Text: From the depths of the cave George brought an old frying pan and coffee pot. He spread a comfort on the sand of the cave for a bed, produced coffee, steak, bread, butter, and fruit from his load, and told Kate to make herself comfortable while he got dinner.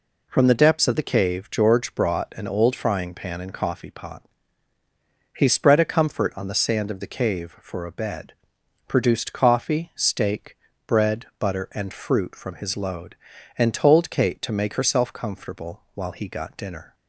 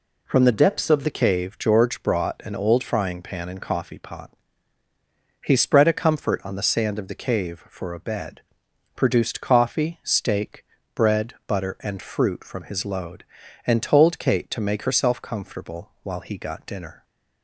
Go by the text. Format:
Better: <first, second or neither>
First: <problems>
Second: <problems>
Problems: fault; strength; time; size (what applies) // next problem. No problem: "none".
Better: first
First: none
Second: changes voice from "depths" to "of"; from 0.5 to 1.0 s; 0.5 s long